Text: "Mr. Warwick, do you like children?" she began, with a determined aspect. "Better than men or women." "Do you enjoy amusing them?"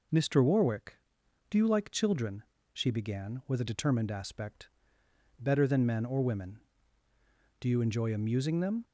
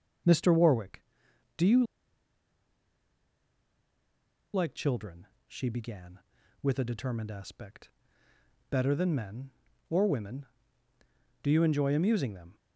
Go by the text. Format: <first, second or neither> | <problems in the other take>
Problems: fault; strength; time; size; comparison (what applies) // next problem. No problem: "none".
first | starts louder than the rest; noticeable; until 1.8 s; 6 dB // pauses between "you" and "like"; strong; at 1.8 s; 2.7 s long